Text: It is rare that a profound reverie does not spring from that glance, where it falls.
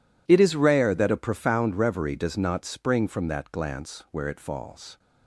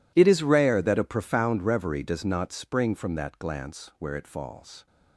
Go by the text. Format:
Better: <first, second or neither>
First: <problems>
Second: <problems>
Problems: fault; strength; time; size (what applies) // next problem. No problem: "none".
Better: first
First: none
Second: gets quieter; strong; throughout; 20.5 dB